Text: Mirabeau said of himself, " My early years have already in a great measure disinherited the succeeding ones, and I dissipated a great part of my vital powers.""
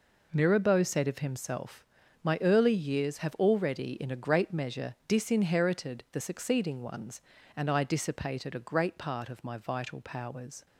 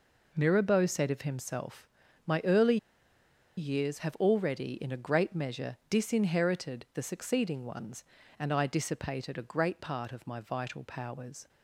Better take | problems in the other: first | pauses between "early" and "years"; noticeable; at 2.7 s; 0.80 s long

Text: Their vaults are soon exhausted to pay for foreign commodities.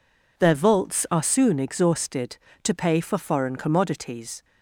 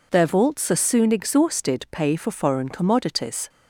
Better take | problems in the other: first | skips "to"; at 1.8 s

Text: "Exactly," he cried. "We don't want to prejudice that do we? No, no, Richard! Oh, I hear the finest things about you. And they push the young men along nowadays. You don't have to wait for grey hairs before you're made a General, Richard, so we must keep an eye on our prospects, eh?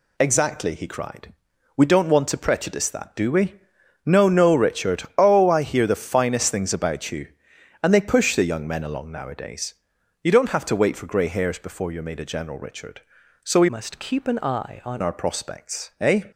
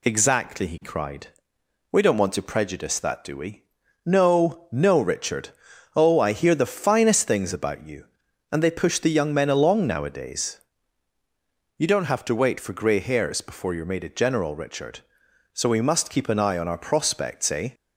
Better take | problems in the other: second | changes voice from "must" to "on"; from 13.6 to 14.9 s; 1.3 s long

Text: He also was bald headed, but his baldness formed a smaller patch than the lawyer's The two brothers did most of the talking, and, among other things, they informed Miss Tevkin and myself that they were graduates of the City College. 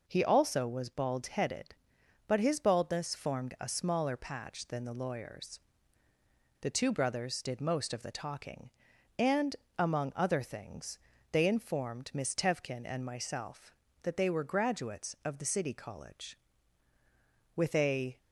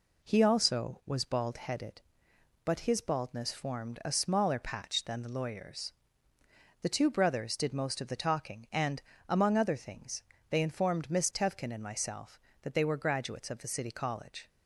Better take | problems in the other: second | pauses between "lawyer's" and "The"; at 5.5 s; 1.0 s long; noticeable in the second // goes on to say "With a"; noticeable; from 17.5 s on; 0.62 s long

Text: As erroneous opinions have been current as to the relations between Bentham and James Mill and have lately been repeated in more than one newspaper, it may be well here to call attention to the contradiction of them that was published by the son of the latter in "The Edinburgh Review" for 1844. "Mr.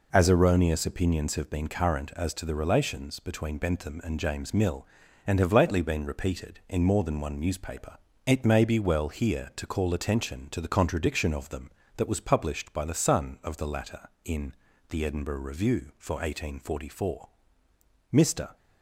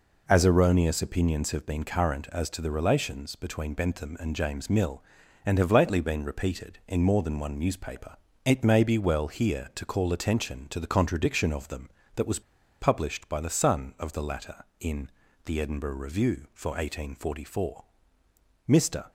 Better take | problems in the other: first | pauses between "was" and "published"; at 12.4 s; 0.39 s long // pauses between "in" and "The"; at 15.0 s; 0.38 s long; also in the first

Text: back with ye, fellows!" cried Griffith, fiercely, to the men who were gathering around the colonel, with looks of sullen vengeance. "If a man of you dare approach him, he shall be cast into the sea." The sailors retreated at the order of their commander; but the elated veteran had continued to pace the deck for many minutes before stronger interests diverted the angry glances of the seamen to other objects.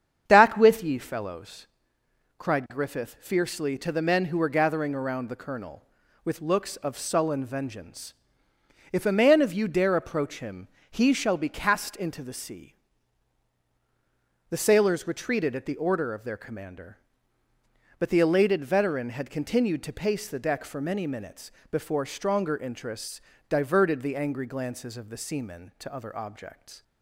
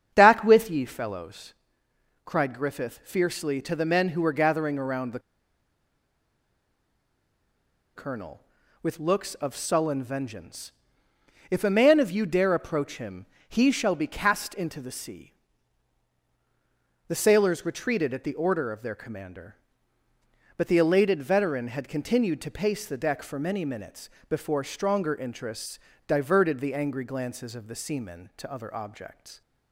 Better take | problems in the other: first | starts louder than the rest; strong; until 1.1 s; 8 dB; strong in the first // pauses between "the" and "colonel"; strong; at 5.1 s; 2.7 s long // pauses between "minutes" and "before"; slight; at 24.0 s; 0.20 s long; slight in the first // pauses between "interests" and "diverted"; slight; at 25.7 s; 0.28 s long; slight in the first

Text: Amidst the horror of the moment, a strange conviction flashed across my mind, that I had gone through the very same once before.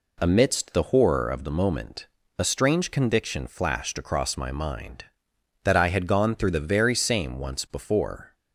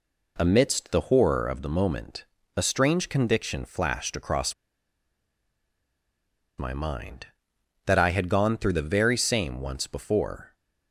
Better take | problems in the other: first | pauses between "across" and "my"; strong; at 4.5 s; 2.0 s long

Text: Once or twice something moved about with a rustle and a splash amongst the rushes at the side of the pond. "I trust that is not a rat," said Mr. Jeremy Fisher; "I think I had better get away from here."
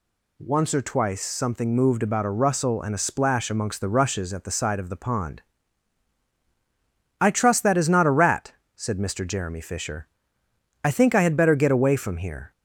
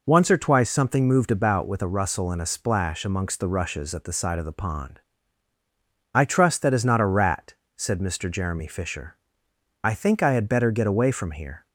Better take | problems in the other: second | skips "with"; at 2.2 s

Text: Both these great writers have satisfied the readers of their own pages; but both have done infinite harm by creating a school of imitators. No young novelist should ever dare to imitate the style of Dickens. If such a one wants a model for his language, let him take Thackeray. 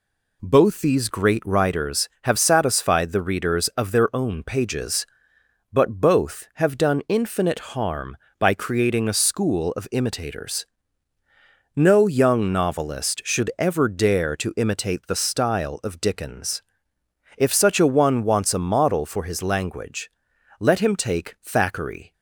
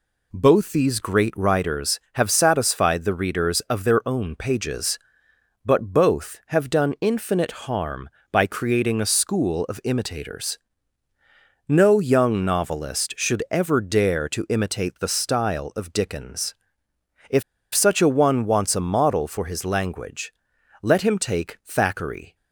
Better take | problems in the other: first | pauses between "If" and "such"; slight; at 17.4 s; 0.32 s long

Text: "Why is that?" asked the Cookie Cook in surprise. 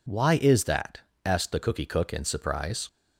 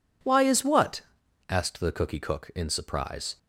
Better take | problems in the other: first | says "what" for "that"; at 0.6 s

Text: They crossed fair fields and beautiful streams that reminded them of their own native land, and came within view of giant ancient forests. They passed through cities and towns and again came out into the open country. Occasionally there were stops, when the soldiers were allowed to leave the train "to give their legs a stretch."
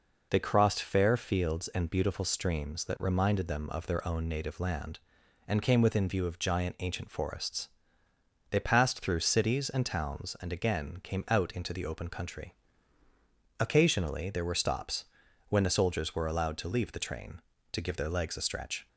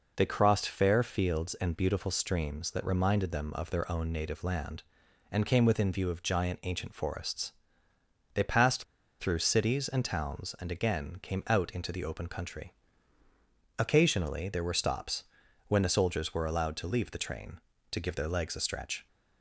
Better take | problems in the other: first | pauses between "passed" and "through"; at 8.8 s; 0.36 s long

